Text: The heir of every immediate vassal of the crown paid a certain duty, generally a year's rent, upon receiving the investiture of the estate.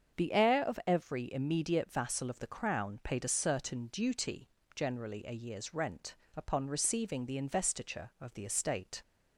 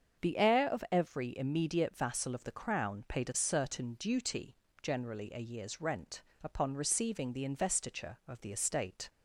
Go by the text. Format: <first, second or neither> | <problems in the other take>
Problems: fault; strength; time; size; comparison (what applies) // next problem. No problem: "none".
neither | starts louder than the rest; the same in both